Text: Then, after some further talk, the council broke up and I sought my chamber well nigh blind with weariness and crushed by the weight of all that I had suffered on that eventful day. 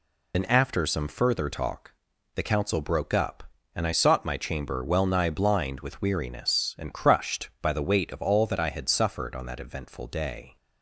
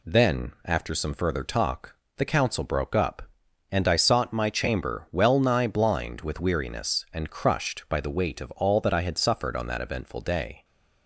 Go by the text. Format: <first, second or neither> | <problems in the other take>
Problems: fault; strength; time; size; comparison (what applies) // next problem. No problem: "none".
second | loses the start of "Then"; at 0.3 s; 55 ms